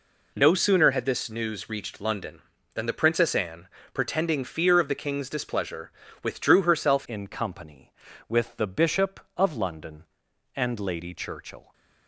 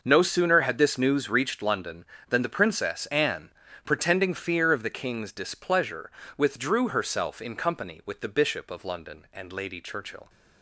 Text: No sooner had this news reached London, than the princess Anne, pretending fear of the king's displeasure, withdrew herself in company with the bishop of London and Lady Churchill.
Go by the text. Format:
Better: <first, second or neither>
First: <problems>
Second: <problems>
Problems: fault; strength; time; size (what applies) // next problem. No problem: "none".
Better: second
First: changes voice at "in"; from 7.0 s on; 4.7 s long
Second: none